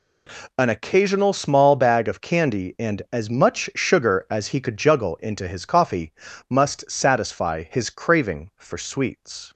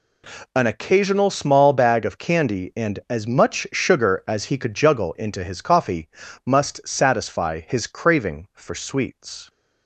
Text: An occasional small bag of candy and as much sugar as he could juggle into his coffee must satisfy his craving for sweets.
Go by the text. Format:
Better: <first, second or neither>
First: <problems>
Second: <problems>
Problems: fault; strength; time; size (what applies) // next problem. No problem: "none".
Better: neither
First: pauses between "coffee" and "must"; at 6.1 s; 0.38 s long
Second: pauses between "coffee" and "must"; at 6.0 s; 0.38 s long